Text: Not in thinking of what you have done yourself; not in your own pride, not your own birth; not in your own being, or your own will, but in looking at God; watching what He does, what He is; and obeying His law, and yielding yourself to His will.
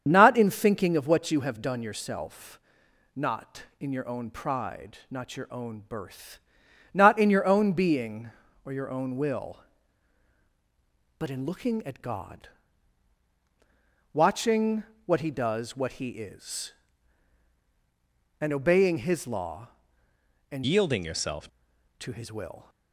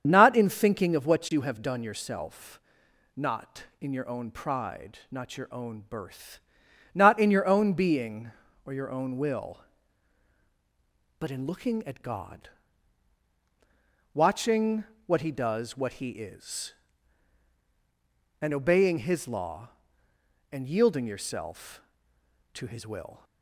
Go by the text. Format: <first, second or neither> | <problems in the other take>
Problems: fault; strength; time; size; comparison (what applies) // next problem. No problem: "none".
second | starts louder than the rest; strong; until 1.0 s; 7.5 dB; strong in the second // pauses between "watching" and "what"; slight; at 14.8 s; 0.22 s long; slight in the second // changes voice from "yielding" to "yourself"; from 20.6 to 21.4 s; 0.8 s long